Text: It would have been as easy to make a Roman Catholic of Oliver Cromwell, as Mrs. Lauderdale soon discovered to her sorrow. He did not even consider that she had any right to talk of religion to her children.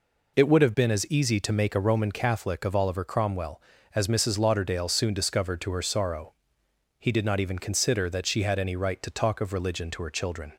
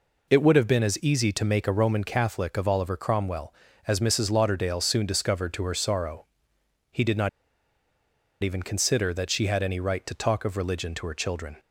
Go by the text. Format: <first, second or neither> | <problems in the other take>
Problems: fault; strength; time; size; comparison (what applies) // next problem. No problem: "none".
first | pauses between "not" and "even"; at 7.2 s; 1.1 s long